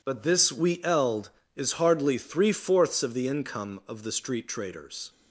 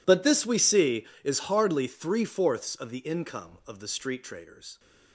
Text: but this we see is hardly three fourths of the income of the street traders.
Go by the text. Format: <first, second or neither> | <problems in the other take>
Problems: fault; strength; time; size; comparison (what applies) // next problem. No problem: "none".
second | says "eld" for "see"; at 0.8 s